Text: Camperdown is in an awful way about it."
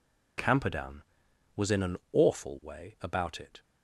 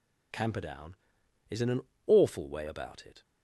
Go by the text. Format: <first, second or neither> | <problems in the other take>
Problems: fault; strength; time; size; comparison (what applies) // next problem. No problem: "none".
second | says "was" for "is"; at 1.5 s // pauses between "an" and "awful"; slight; at 1.9 s; 0.16 s long; slight in the second